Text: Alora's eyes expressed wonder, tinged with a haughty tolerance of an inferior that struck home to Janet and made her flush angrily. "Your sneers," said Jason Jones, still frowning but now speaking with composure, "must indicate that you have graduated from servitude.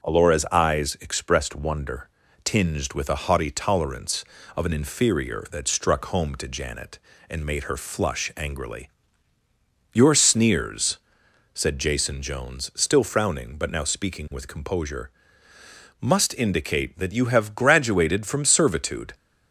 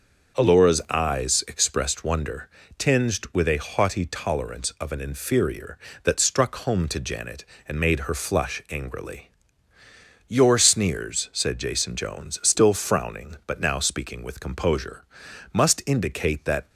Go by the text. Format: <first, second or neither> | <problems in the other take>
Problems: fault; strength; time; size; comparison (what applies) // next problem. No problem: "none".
first | stops before "you have graduated from servitude"; at 16.6 s